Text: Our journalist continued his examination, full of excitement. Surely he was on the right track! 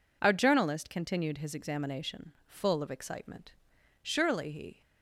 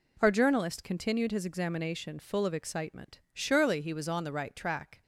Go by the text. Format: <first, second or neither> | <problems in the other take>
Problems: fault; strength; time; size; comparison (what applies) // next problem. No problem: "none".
second | stops before "was on the right track"; at 4.8 s